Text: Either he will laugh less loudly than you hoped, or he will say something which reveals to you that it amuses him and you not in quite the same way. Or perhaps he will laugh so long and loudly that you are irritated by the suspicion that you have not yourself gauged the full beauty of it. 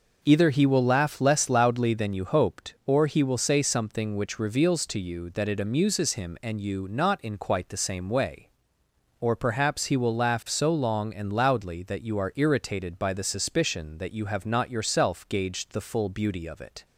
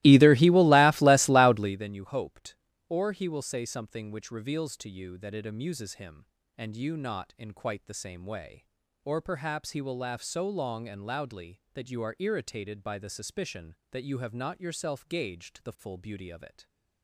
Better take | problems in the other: first | starts louder than the rest; strong; until 1.9 s; 18.5 dB

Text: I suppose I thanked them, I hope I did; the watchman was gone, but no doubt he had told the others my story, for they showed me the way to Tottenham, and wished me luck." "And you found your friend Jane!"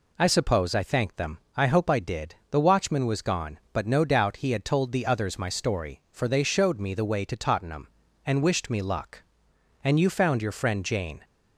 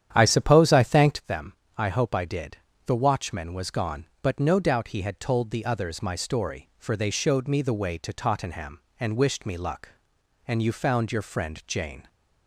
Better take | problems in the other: first | starts louder than the rest; strong; until 1.3 s; 10 dB

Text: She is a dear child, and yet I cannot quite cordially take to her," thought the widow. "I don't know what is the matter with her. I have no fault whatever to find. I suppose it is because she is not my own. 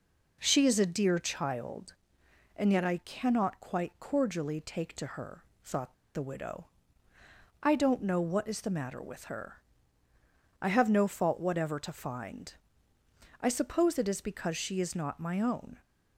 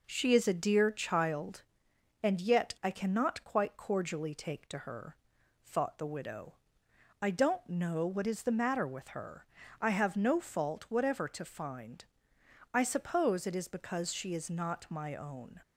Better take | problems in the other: second | pauses between "thought" and "the"; slight; at 5.9 s; 0.19 s long

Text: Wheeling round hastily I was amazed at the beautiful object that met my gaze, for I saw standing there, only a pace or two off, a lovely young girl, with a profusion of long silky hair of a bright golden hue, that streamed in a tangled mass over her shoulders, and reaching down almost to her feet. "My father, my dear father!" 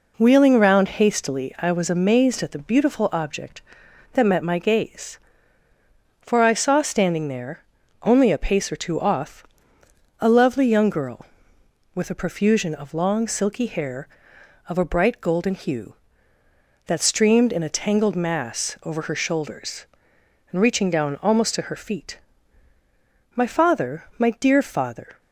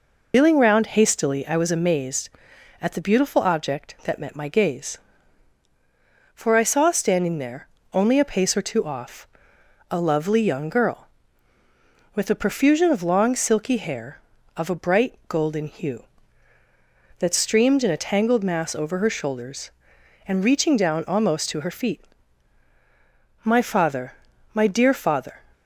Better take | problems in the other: first | loses the start of "Wheeling"; at 0.3 s; 85 ms

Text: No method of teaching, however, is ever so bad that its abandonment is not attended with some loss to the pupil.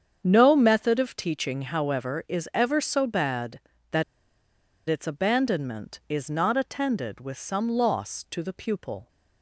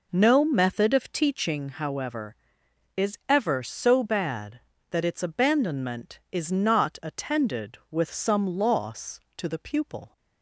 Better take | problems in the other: second | starts louder than the rest; strong; until 1.2 s; 7.5 dB // pauses between "that" and "its"; noticeable; at 4.0 s; 0.86 s long

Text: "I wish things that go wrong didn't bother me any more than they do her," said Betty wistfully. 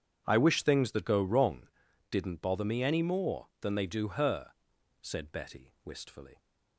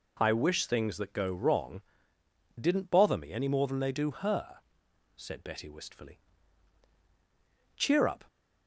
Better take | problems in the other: first | pauses between "wrong" and "didn't"; noticeable; at 1.8 s; 0.78 s long; also in the first // goes on to say "Cheer up"; slight; from 7.7 s on; 0.48 s long

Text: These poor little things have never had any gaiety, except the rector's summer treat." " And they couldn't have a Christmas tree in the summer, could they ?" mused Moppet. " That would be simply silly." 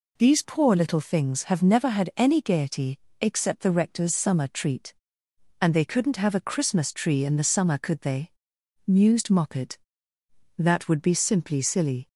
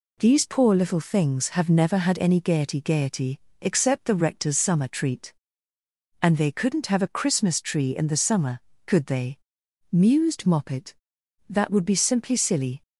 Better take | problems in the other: first | says "gaiety" twice; at 2.7 s

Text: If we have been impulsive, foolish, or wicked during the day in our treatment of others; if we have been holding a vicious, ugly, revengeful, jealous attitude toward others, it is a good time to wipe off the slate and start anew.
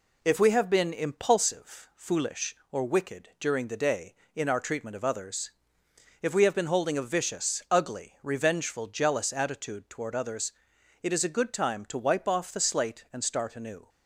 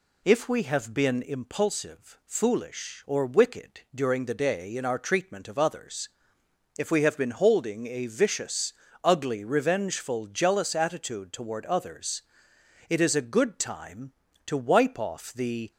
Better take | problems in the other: first | stops before "slate and start anew"; at 15.7 s

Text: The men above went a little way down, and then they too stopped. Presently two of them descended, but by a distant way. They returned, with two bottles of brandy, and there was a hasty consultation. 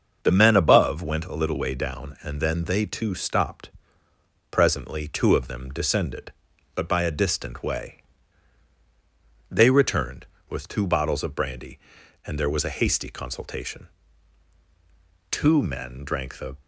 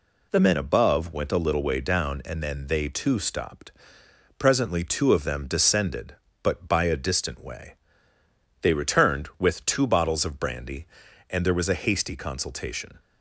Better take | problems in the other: second | starts louder than the rest; until 1.2 s; 6.5 dB // goes on to say "Two men drank the"; noticeable; from 15.3 s on; 1.2 s long

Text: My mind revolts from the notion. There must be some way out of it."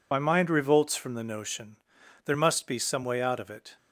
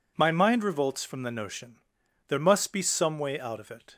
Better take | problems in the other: second | loses the start of "My"; at 0.1 s; 45 ms

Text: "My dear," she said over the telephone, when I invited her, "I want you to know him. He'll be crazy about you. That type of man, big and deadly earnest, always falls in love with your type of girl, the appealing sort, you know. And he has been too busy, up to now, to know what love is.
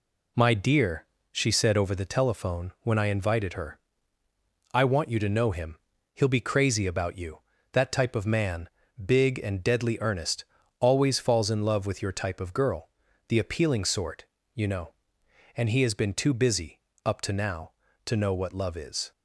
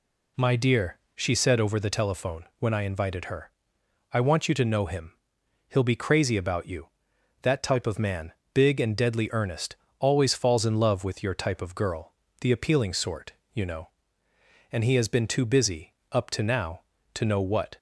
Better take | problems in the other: first | stops before "love is"; at 17.7 s

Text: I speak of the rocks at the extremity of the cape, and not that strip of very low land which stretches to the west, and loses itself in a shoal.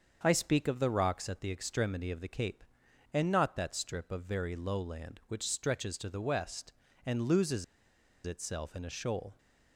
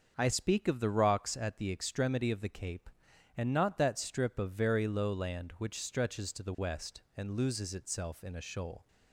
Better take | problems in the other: second | starts louder than the rest; until 1.2 s; 6.5 dB; also in the second // pauses between "loses" and "itself"; noticeable; at 7.6 s; 0.60 s long

